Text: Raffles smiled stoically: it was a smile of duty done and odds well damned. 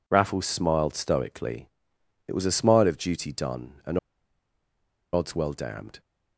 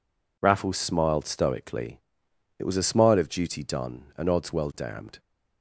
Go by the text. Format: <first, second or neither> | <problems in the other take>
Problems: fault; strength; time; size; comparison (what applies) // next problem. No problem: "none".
second | pauses between "and" and "odds"; at 3.9 s; 1.1 s long